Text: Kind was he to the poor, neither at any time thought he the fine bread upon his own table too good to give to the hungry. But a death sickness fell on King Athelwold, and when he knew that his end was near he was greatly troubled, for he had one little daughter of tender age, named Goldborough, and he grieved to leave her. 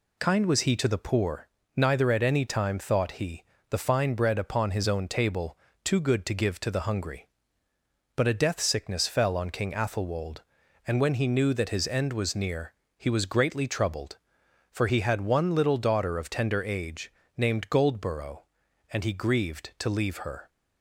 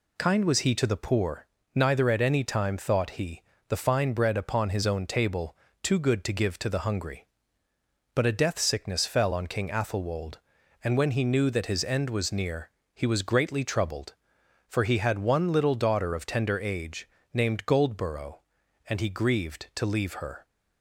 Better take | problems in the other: neither | pauses between "he" and "the"; slight; the same in both // pauses between "table" and "too"; slight; the same in both // pauses between "near" and "he"; slight; the same in both

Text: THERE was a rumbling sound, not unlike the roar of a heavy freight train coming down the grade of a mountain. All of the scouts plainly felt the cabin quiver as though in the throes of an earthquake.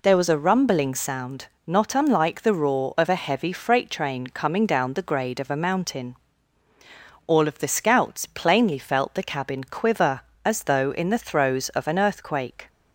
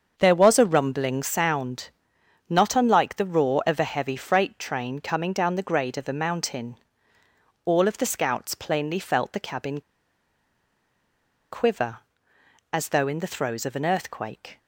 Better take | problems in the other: first | starts louder than the rest; until 1.1 s; 7 dB // pauses between "cabin" and "quiver"; strong; at 9.7 s; 1.7 s long

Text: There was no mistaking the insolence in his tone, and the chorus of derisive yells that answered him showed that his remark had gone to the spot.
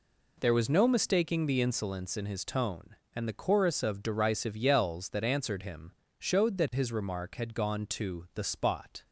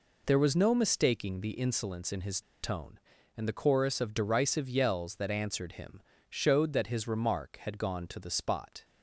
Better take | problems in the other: first | pauses between "his" and "tone"; slight; at 2.4 s; 0.21 s long // pauses between "him" and "showed"; slight; at 6.0 s; 0.26 s long; slight in the first

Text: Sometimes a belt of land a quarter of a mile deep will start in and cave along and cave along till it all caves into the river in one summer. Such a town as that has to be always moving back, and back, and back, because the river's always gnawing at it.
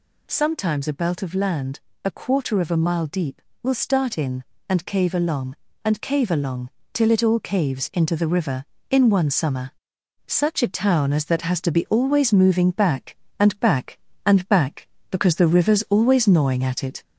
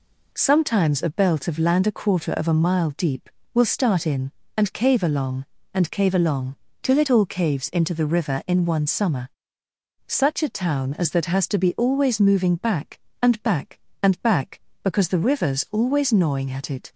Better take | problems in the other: second | gets louder; slight; throughout; 3 dB // pauses between "land" and "a"; slight; at 1.7 s; 0.26 s long // pauses between "along" and "till"; slight; at 6.6 s; 0.24 s long; slight in the second

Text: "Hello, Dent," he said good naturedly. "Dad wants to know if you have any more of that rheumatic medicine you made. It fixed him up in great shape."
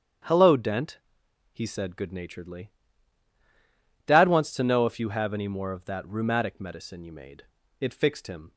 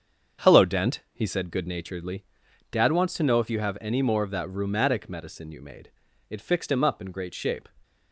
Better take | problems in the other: second | starts louder than the rest; strong; until 1.7 s; 8.5 dB; also in the second // stops before "up in great shape"; at 8.5 s

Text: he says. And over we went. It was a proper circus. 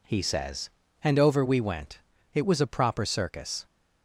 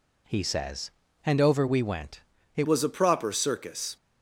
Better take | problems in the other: first | changes voice at "was"; from 2.6 s on; 1.3 s long

